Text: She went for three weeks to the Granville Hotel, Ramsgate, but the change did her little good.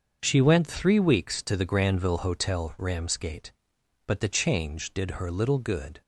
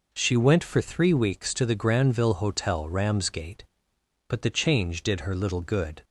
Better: second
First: starts louder than the rest; until 1.2 s; 6.5 dB // skips "for"; at 0.6 s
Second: none

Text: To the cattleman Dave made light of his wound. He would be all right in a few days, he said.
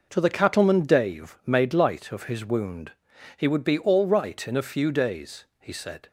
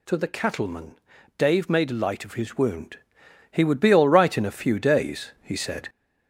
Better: first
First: none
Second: gets louder; noticeable; throughout; 5 dB // pauses between "cattleman" and "Dave"; at 0.9 s; 0.38 s long

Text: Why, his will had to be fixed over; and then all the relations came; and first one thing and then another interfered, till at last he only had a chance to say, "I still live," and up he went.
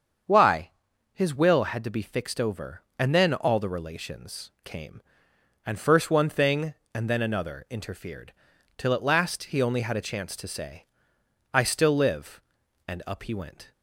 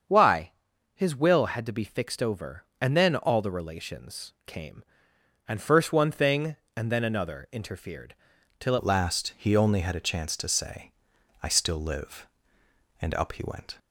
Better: first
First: starts louder than the rest; until 1.7 s; 7 dB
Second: starts louder than the rest; strong; until 1.5 s; 7 dB // changes voice at "at"; from 8.7 s on; 5.0 s long

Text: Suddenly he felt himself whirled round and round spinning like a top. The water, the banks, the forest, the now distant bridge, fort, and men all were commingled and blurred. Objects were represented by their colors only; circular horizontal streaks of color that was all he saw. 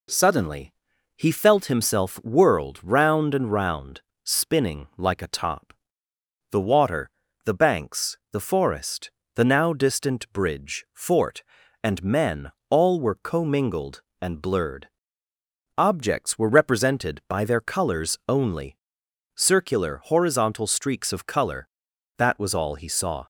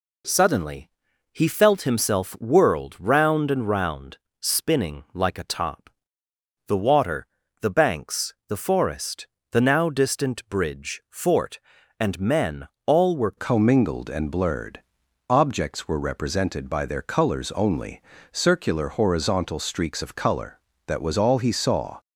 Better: first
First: pauses between "Suddenly" and "he"; at 0.7 s; 0.42 s long // pauses between "round" and "spinning"; slight; at 4.0 s; 0.22 s long // pauses between "men" and "all"; slight; at 12.5 s; 0.20 s long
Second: pauses between "Suddenly" and "he"; at 0.8 s; 0.42 s long // pauses between "round" and "spinning"; slight; at 4.1 s; 0.22 s long // pauses between "men" and "all"; slight; at 12.6 s; 0.20 s long // changes voice at "commingled"; from 13.3 s on; 8.6 s long

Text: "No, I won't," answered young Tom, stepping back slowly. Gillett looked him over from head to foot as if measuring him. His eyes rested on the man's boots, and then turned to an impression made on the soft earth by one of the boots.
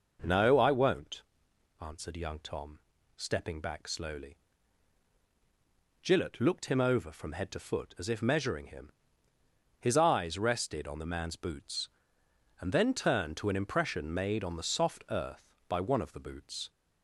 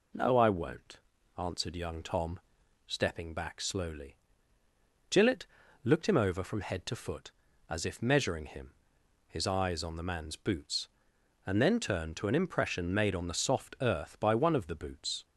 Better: first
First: none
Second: pauses between "Gillett" and "looked"; at 5.4 s; 0.40 s long // skips "rested"; at 9.8 s

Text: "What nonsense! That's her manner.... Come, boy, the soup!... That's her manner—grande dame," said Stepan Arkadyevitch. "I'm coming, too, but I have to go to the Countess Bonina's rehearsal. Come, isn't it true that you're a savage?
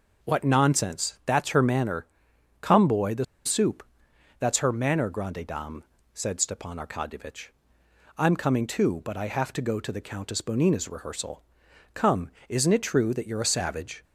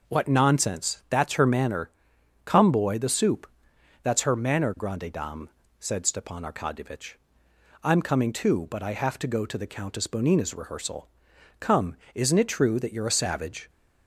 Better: second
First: pauses between "the" and "soup"; slight; at 3.2 s; 0.20 s long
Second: none

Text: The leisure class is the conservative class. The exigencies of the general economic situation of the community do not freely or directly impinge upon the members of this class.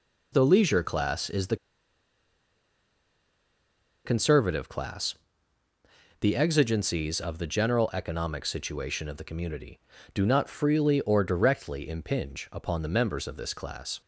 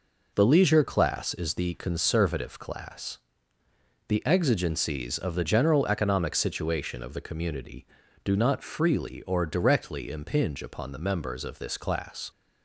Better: second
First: pauses between "the" and "conservative"; strong; at 1.5 s; 2.4 s long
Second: none

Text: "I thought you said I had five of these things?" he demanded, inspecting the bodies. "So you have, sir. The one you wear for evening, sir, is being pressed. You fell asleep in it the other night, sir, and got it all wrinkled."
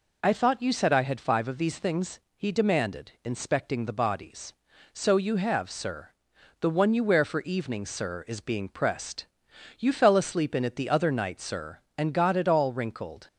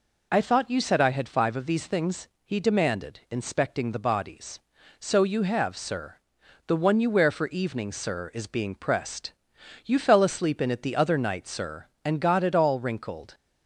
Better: neither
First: none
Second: none

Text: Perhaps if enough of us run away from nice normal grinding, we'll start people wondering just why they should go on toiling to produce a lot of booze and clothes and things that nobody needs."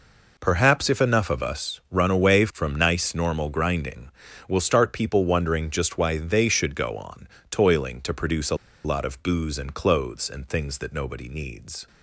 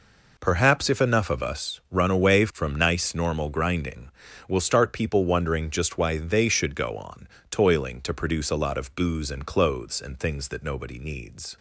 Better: second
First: pauses between "on" and "toiling"; slight; at 7.2 s; 0.24 s long // pauses between "a" and "lot"; slight; at 8.5 s; 0.29 s long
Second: pauses between "on" and "toiling"; slight; at 7.2 s; 0.24 s long

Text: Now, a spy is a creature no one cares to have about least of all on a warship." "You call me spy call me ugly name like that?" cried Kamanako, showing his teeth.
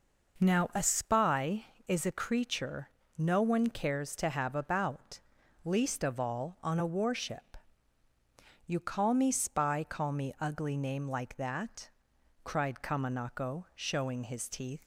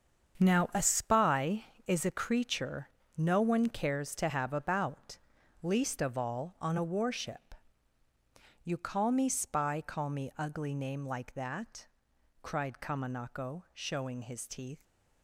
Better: first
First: pauses between "creature" and "no"; slight; at 2.9 s; 0.26 s long // pauses between "about" and "least"; noticeable; at 5.1 s; 0.46 s long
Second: gets quieter; strong; throughout; 10.5 dB // pauses between "creature" and "no"; slight; at 2.9 s; 0.26 s long // pauses between "about" and "least"; noticeable; at 5.1 s; 0.46 s long

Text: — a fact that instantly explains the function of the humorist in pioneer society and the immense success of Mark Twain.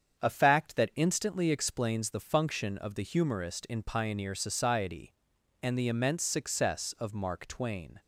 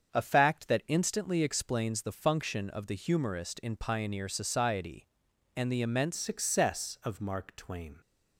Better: first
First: starts louder than the rest; strong; until 1.2 s; 7.5 dB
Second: starts louder than the rest; strong; until 1.1 s; 7 dB // changes voice at "success"; from 6.1 s on; 1.8 s long

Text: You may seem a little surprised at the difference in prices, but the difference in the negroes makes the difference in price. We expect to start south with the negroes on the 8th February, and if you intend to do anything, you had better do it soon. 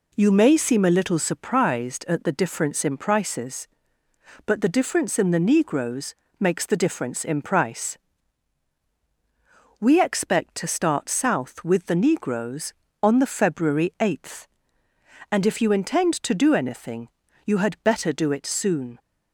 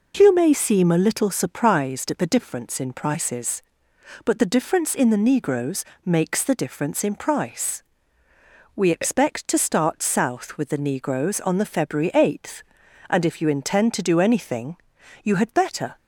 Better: first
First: pauses between "negroes" and "makes"; slight; at 6.1 s; 0.24 s long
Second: pauses between "negroes" and "makes"; slight; at 5.8 s; 0.22 s long // stops before "do it soon"; at 15.9 s

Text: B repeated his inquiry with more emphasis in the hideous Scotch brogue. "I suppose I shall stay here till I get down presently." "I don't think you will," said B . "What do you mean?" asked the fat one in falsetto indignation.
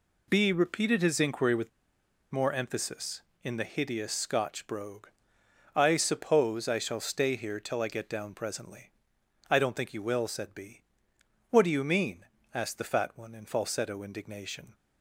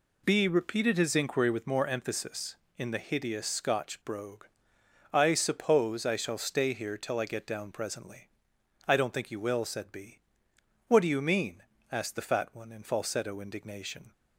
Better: second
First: pauses between "with" and "more"; noticeable; at 1.6 s; 0.62 s long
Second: none

